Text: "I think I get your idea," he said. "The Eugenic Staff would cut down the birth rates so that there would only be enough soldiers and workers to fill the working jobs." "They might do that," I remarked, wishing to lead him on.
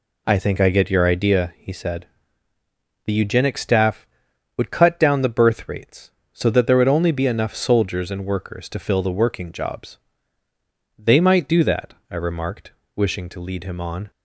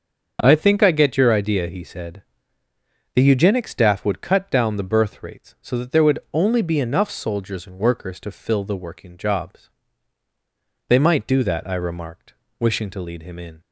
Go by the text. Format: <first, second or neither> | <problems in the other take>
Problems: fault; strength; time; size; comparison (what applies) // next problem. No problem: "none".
first | starts louder than the rest; until 1.4 s; 7 dB // says "in" for "on"; at 13.3 s